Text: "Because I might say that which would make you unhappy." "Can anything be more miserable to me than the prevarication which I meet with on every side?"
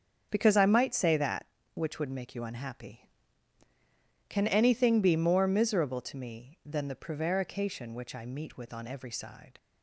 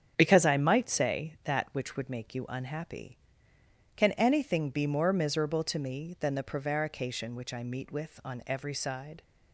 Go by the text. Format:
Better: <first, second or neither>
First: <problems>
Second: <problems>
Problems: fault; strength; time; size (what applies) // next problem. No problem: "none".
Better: neither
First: starts louder than the rest; strong; until 1.3 s; 7 dB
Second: starts louder than the rest; strong; until 1.1 s; 8.5 dB